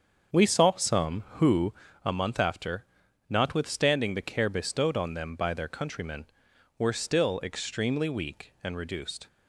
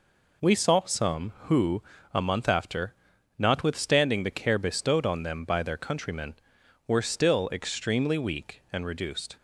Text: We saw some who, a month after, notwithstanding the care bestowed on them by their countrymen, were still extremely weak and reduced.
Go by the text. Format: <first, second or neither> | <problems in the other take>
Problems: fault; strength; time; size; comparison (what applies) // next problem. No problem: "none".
second | starts louder than the rest; strong; until 1.9 s; 7 dB